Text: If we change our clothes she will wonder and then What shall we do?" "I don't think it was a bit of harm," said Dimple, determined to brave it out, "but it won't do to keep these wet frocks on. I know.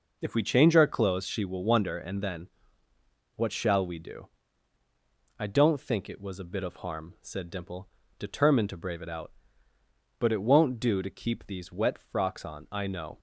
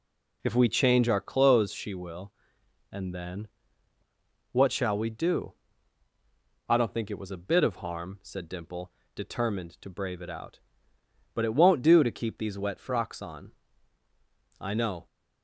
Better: first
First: pauses between "then" and "What"; noticeable; at 2.4 s; 0.86 s long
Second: skips "wonder"; at 2.6 s // pauses between "then" and "What"; at 3.4 s; 1.0 s long

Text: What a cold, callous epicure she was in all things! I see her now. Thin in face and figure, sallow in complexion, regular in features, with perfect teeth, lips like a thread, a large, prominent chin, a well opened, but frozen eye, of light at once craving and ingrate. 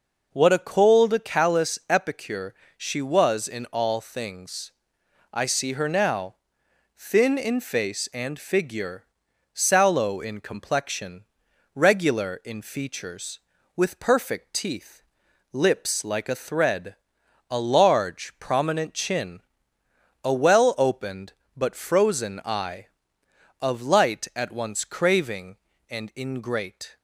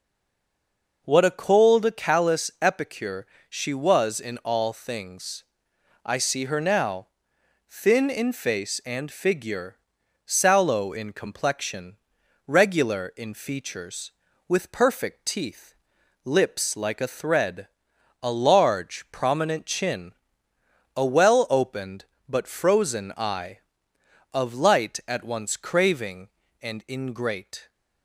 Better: first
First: pauses between "epicure" and "she"; slight; at 2.5 s; 0.22 s long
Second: stays silent before the first word; until 1.0 s; 1.0 s long // pauses between "epicure" and "she"; slight; at 3.2 s; 0.22 s long

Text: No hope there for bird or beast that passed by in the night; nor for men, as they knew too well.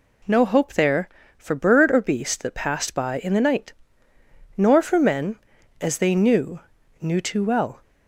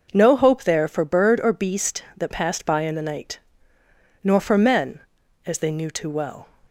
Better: second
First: says "knew" twice; at 7.0 s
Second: none

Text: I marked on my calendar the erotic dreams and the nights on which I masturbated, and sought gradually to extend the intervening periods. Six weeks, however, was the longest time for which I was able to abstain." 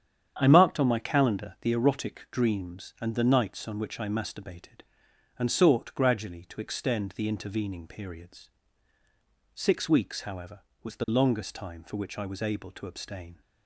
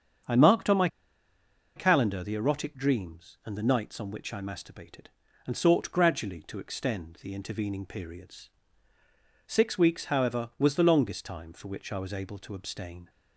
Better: first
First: starts louder than the rest; strong; until 1.3 s; 8.5 dB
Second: starts louder than the rest; strong; until 2.1 s; 7.5 dB // pauses between "my" and "calendar"; noticeable; at 0.8 s; 0.88 s long

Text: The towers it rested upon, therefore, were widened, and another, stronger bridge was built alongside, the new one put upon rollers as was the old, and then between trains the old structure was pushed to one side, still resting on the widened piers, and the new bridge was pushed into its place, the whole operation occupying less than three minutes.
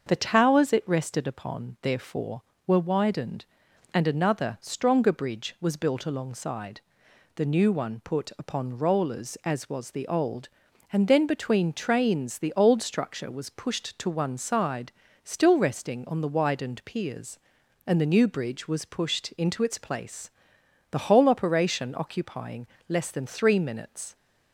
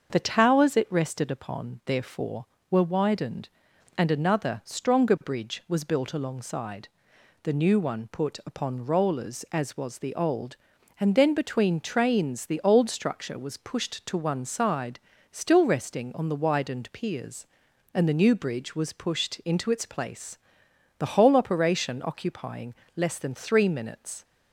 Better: neither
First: starts louder than the rest; until 1.0 s; 6.5 dB // pauses between "occupying" and "less"; slight; at 22.6 s; 0.24 s long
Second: starts louder than the rest; until 1.1 s; 6.5 dB // pauses between "occupying" and "less"; slight; at 22.7 s; 0.24 s long

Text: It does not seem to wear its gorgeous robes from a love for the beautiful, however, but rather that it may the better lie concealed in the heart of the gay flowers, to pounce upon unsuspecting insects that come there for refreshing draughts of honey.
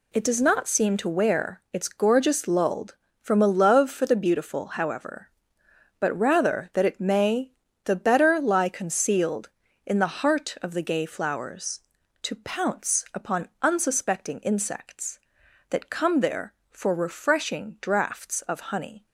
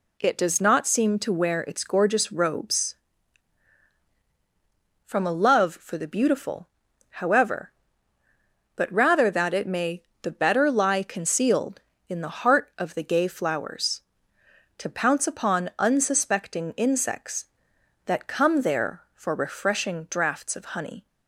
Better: second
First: says "lulled" for "robes"; at 2.4 s // pauses between "may" and "the"; slight; at 7.5 s; 0.34 s long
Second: pauses between "may" and "the"; slight; at 10.0 s; 0.22 s long

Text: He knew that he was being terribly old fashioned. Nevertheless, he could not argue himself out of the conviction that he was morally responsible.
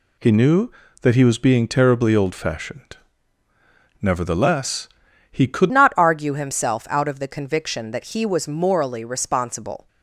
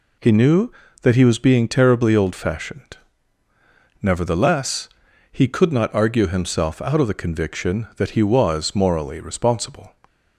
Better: second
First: changes voice at "not"; from 5.7 s on; 4.1 s long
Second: none

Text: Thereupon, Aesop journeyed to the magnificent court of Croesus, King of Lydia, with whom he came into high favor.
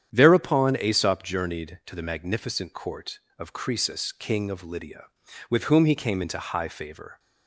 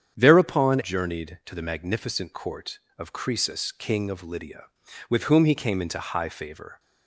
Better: first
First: starts louder than the rest; strong; until 1.1 s; 9 dB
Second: starts louder than the rest; strong; until 1.1 s; 8 dB // skips "Aesop"; at 0.8 s

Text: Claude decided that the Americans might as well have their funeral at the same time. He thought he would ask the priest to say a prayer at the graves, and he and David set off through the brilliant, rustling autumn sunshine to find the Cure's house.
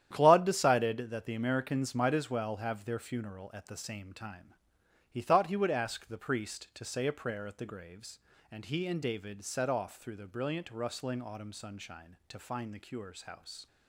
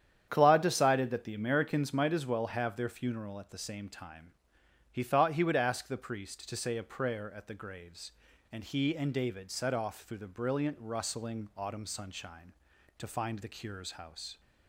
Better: neither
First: starts louder than the rest; strong; until 1.1 s; 10.5 dB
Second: starts louder than the rest; strong; until 1.2 s; 9 dB

